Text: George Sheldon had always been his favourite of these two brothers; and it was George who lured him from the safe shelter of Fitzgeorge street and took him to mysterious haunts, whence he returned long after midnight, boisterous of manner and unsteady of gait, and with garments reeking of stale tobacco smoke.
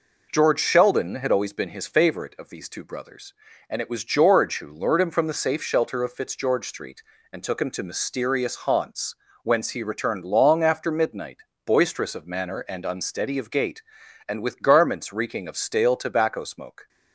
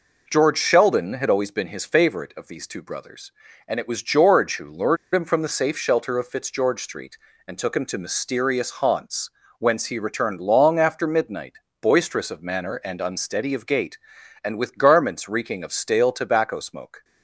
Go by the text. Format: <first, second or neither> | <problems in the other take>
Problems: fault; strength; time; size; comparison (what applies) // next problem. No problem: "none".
first | pauses between "lured" and "him"; slight; at 4.9 s; 0.17 s long